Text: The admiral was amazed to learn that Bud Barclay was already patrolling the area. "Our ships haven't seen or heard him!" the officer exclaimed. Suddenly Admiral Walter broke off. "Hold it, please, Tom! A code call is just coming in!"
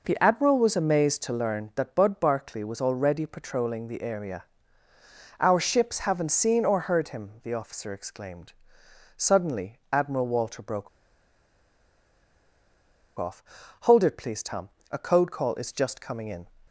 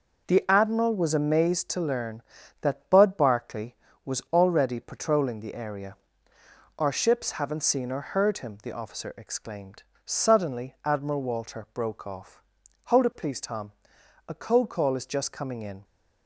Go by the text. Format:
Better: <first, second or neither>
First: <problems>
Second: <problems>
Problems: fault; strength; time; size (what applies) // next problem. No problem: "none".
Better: second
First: pauses between "broke" and "off"; strong; at 10.8 s; 2.3 s long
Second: none